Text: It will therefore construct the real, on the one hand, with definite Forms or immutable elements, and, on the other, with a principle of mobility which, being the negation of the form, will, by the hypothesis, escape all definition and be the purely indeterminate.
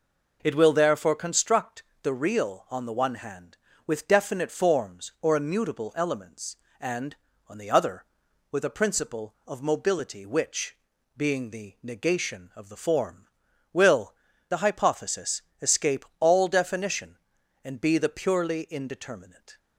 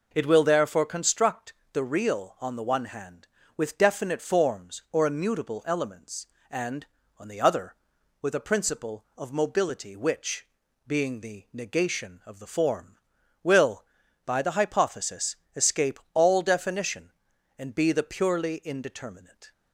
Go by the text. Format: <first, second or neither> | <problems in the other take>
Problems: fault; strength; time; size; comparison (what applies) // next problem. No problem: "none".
second | pauses between "construct" and "the"; slight; at 1.8 s; 0.20 s long; slight in the second // skips "by"; at 14.3 s